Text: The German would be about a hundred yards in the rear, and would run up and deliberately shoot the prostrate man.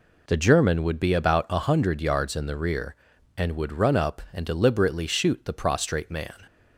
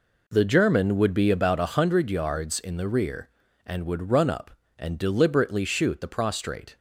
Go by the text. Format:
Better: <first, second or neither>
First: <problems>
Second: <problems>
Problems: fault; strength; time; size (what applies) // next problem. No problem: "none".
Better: first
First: none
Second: stops before "man"; at 6.7 s